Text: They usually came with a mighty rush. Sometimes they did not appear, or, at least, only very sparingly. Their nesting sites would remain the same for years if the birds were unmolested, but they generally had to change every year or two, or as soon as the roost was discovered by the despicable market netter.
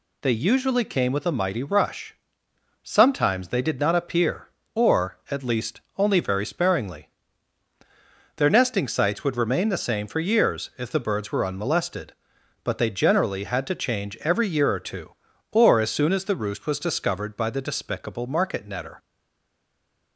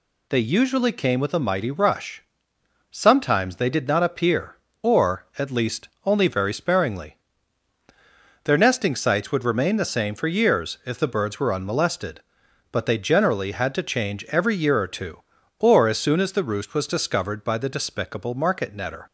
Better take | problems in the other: second | stays silent after the last word; from 18.9 s on; 1.2 s long

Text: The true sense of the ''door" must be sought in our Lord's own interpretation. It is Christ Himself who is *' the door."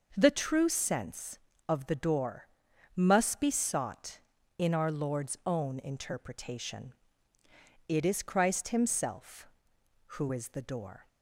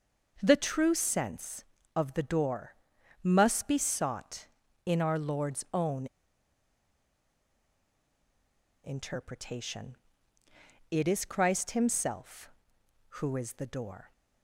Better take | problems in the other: first | pauses between "door" and "must"; noticeable; at 2.7 s; 0.48 s long; noticeable in the first // pauses between "own" and "interpretation"; strong; at 6.0 s; 2.7 s long

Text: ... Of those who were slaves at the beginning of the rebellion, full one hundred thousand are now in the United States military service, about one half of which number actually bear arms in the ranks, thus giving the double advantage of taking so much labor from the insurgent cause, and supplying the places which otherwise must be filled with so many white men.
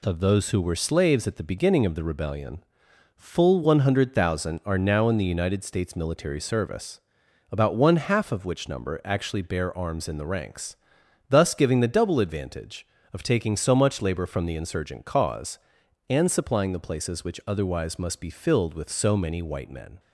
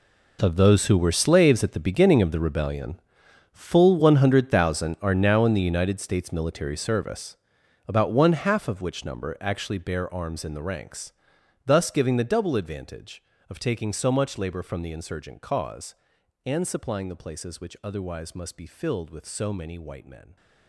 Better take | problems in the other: first | gets quieter; strong; throughout; 15 dB

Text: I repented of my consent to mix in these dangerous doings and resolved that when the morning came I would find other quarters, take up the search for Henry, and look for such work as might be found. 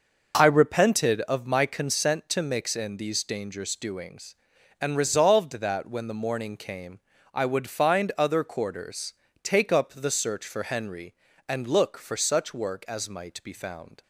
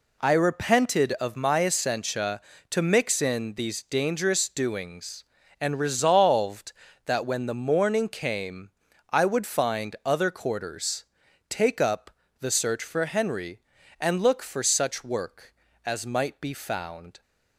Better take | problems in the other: first | says "essentia" for "consent"; at 1.6 s // pauses between "came" and "I"; at 8.7 s; 0.40 s long; slight in the first // pauses between "up" and "the"; slight; at 12.1 s; 0.30 s long

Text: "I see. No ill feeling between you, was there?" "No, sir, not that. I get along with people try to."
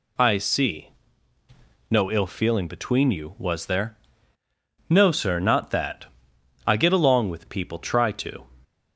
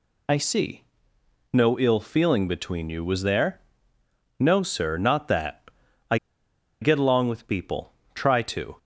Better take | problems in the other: first | pauses between "I" and "get"; noticeable; at 6.1 s; 0.64 s long // pauses between "people" and "try"; slight; at 7.9 s; 0.22 s long

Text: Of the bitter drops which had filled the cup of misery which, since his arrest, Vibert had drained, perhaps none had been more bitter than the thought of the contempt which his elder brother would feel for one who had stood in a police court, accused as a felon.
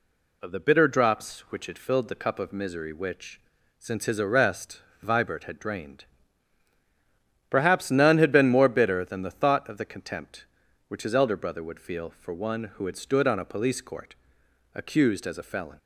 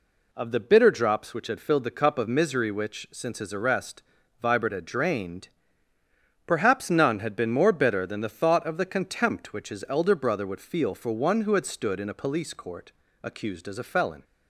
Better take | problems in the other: second | says "on" for "in"; at 13.2 s

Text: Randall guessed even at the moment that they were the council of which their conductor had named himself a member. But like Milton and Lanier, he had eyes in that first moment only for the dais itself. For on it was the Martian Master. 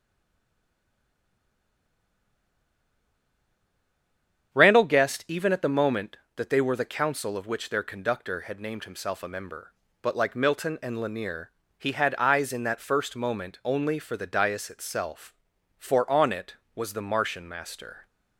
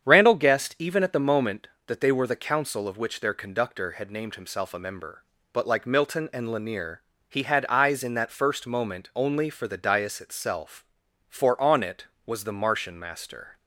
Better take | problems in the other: second | stays silent before the first word; strong; until 4.5 s; 4.5 s long // starts louder than the rest; strong; until 5.5 s; 8 dB; strong in the second

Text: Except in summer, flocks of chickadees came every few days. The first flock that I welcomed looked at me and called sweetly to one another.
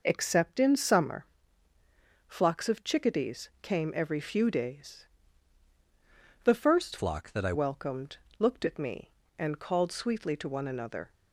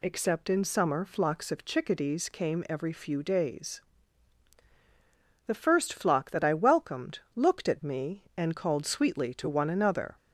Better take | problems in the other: second | changes voice from "flock" to "I"; from 6.9 to 7.5 s; 0.6 s long // pauses between "welcomed" and "looked"; slight; at 8.1 s; 0.24 s long; slight in the second

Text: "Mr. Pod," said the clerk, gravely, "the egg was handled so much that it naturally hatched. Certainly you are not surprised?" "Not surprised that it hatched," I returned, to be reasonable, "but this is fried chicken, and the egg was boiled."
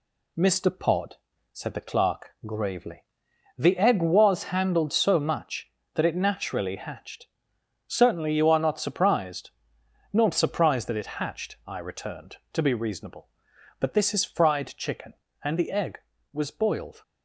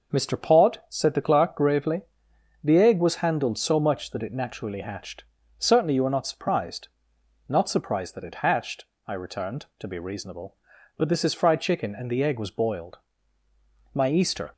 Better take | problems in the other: first | goes on to say "My Easter"; from 13.9 s on; 0.58 s long

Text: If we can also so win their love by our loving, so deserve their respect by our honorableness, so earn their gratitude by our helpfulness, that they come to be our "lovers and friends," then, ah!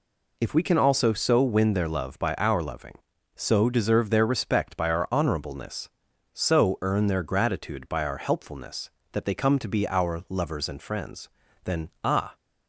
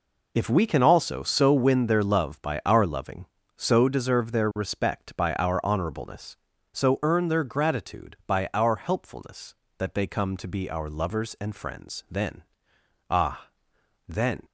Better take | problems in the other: first | goes on to say "then"; slight; from 14.0 s on; 0.36 s long

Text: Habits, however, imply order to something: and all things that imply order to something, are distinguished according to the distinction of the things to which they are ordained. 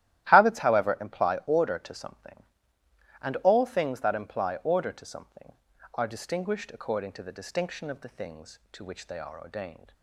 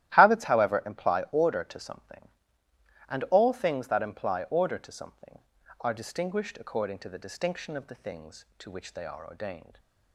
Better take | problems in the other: neither | starts louder than the rest; strong; the same in both

